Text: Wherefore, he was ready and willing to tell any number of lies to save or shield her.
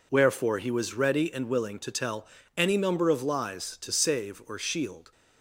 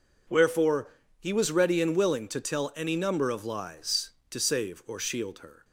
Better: second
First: pauses between "tell" and "any"; slight; at 2.2 s; 0.32 s long // stops before "her"; at 5.1 s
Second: none

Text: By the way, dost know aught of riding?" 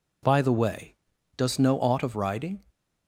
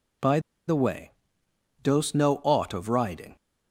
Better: first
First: none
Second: pauses between "By" and "the"; slight; at 0.3 s; 0.28 s long

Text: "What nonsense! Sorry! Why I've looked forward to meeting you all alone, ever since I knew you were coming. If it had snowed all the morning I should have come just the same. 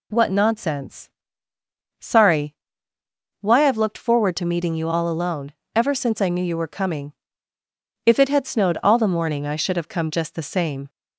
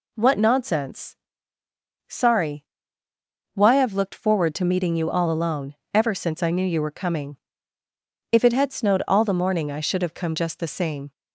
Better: neither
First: none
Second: none

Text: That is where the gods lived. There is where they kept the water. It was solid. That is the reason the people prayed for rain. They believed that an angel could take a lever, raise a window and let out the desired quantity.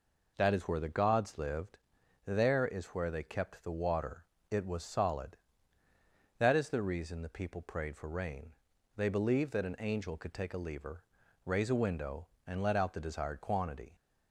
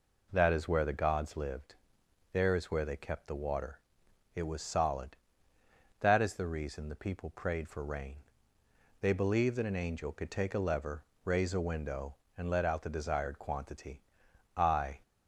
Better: first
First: none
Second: goes on to say "I"; slight; from 14.5 s on; 0.44 s long

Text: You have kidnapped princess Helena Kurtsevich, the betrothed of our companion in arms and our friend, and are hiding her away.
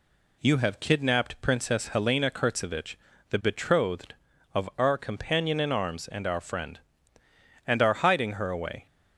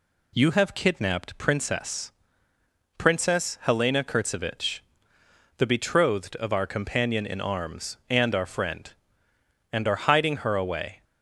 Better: first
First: none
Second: says "princess" twice; at 2.9 s

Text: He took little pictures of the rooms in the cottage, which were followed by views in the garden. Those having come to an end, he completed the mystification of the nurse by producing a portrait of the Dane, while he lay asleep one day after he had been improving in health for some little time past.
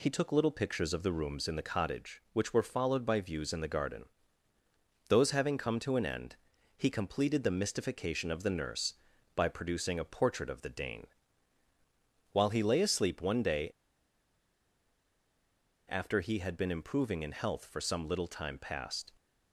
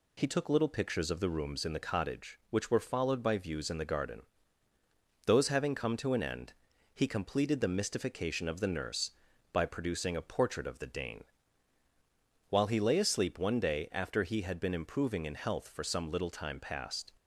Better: second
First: pauses between "day" and "after"; strong; at 13.6 s; 2.2 s long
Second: none

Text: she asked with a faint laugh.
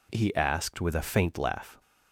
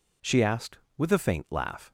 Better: second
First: says "he" for "she"; at 0.1 s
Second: none

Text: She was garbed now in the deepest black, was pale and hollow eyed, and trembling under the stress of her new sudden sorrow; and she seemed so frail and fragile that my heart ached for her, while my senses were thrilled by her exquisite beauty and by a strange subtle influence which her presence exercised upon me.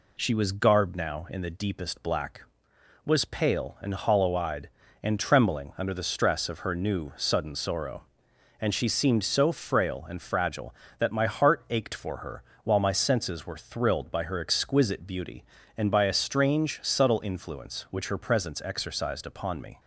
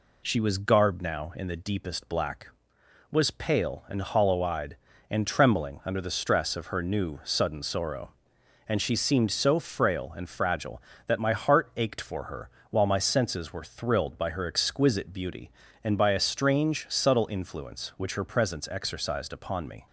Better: neither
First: none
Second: none

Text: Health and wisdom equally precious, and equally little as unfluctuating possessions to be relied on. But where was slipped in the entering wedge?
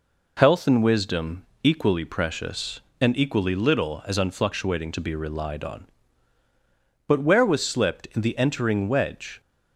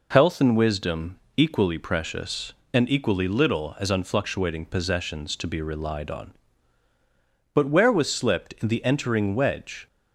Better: second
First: pauses between "wisdom" and "equally"; slight; at 1.4 s; 0.20 s long // skips "possessions"; at 4.9 s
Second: pauses between "wisdom" and "equally"; slight; at 1.1 s; 0.20 s long

